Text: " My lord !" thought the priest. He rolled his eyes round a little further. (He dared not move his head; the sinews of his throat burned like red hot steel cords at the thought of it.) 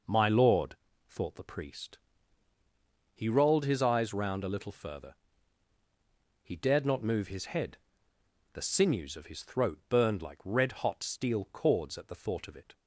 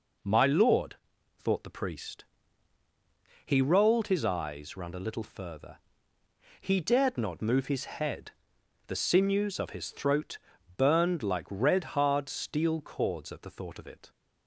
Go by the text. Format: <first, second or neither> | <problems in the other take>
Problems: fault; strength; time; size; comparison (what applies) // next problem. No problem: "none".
first | pauses between "throat" and "burned"; at 10.3 s; 0.38 s long // says "hard" for "hot"; at 11.9 s